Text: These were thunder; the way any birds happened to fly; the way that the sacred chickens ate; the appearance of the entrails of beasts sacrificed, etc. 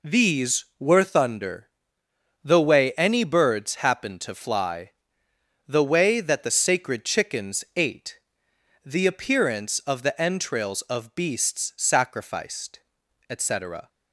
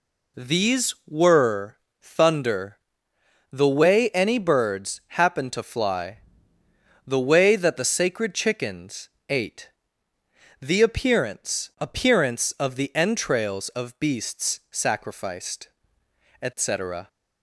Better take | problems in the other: first | pauses between "were" and "thunder"; slight; at 1.7 s; 0.26 s long // pauses between "chickens" and "ate"; slight; at 9.1 s; 0.20 s long // says "appearance" twice; at 11.7 s

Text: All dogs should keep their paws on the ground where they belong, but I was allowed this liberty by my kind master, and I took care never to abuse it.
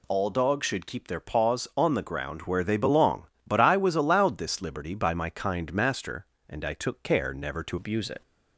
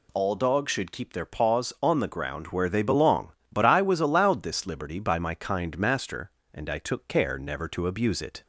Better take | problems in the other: second | changes voice at "abuse"; from 7.7 s on; 0.5 s long

